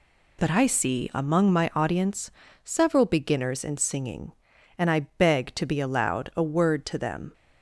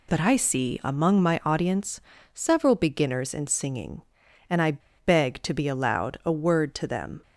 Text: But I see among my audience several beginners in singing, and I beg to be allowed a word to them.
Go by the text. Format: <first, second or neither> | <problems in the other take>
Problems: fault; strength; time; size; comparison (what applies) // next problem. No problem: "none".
first | pauses between "audience" and "several"; slight; at 2.0 s; 0.32 s long; slight in the first // pauses between "I" and "beg"; slight; at 4.7 s; 0.26 s long